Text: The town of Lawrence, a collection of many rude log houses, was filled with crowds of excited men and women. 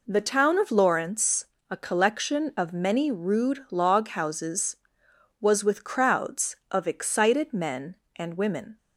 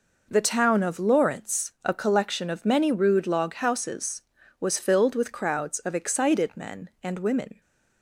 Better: second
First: skips "filled"; at 5.6 s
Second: none

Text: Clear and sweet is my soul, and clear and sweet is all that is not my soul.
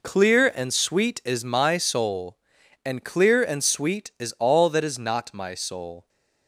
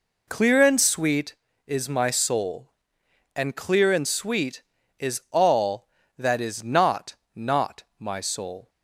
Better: first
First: none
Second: says "not" twice; at 7.3 s

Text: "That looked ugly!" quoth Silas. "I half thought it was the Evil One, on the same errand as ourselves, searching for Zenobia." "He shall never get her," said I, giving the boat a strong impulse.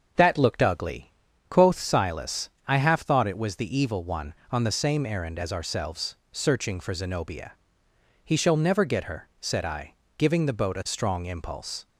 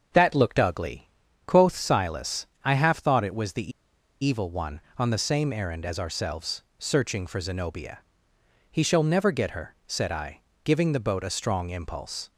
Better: first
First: starts louder than the rest; until 1.5 s; 6.5 dB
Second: starts louder than the rest; until 1.5 s; 6.5 dB // pauses between "the" and "Evil"; noticeable; at 3.7 s; 0.52 s long

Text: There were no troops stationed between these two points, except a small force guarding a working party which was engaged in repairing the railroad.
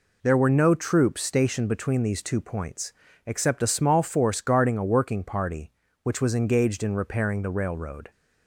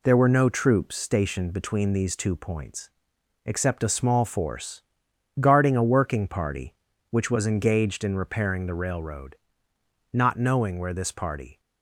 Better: first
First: none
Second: pauses between "force" and "guarding"; noticeable; at 4.8 s; 0.58 s long // goes on to say "Not knowing where this party"; from 10.1 s on; 1.4 s long

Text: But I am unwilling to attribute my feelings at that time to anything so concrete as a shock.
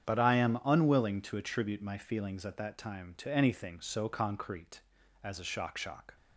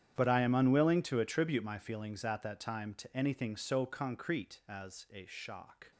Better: second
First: starts louder than the rest; strong; until 1.1 s; 8.5 dB // says "shock" twice; at 5.7 s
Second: starts louder than the rest; strong; until 1.1 s; 9.5 dB

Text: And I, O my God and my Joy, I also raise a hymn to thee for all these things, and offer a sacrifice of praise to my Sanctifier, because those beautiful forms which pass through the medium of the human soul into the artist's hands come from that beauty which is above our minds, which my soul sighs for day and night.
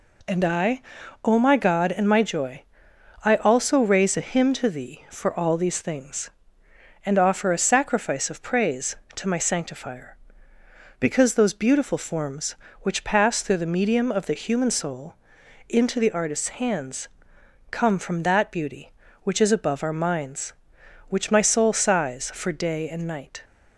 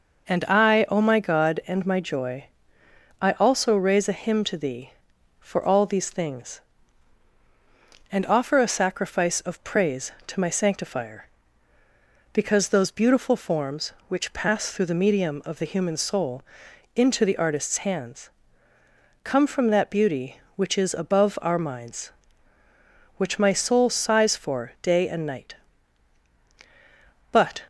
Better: first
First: pauses between "soul" and "into"; noticeable; at 15.1 s; 0.54 s long // pauses between "hands" and "come"; noticeable; at 17.0 s; 0.62 s long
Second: pauses between "soul" and "into"; noticeable; at 16.4 s; 0.52 s long // pauses between "hands" and "come"; noticeable; at 18.3 s; 0.94 s long // goes on to say "But"; slight; from 27.3 s on; 0.30 s long

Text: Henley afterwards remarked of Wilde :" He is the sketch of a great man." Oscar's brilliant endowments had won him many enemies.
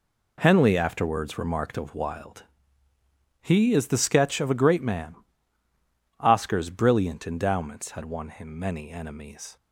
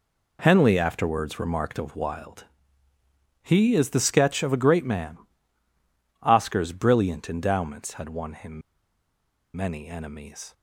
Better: first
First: none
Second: pauses between "him" and "many"; noticeable; at 8.6 s; 0.95 s long

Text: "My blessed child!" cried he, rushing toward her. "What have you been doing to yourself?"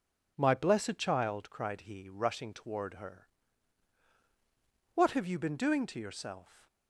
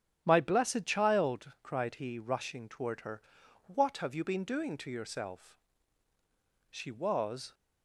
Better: first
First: none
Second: starts louder than the rest; strong; until 1.2 s; 8 dB // goes on to say "She was"; noticeable; from 6.6 s on; 0.84 s long

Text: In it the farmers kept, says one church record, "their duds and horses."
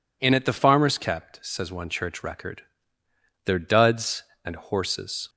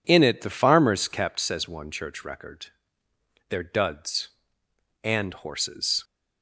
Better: neither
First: none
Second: none

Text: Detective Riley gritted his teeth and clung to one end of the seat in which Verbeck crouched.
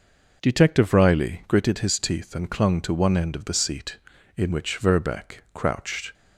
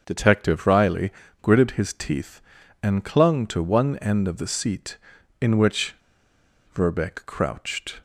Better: first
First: none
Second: starts louder than the rest; until 1.0 s; 6.5 dB // pauses between "Riley" and "gritted"; slight; at 1.1 s; 0.30 s long // pauses between "which" and "Verbeck"; noticeable; at 5.9 s; 0.79 s long

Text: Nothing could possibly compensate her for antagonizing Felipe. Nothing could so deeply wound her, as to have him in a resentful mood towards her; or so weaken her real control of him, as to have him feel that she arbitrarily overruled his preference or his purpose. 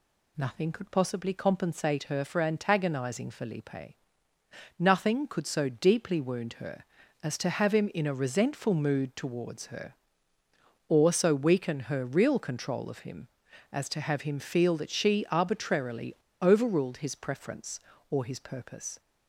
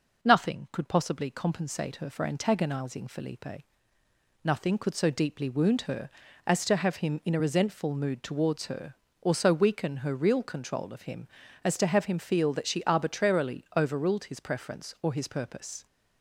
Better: second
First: pauses between "arbitrarily" and "overruled"; slight; at 16.1 s; 0.26 s long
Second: none

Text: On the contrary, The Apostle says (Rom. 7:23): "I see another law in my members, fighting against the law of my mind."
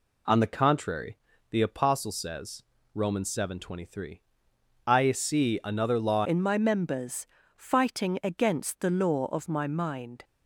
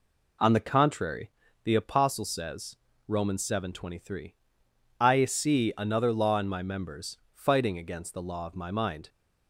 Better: second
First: changes voice at "in"; from 6.2 s on; 4.0 s long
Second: none

